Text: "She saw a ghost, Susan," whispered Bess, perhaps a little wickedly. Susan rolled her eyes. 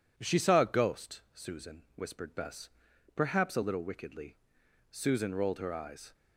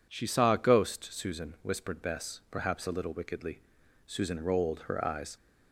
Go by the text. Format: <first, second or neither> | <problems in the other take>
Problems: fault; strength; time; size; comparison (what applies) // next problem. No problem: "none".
neither | none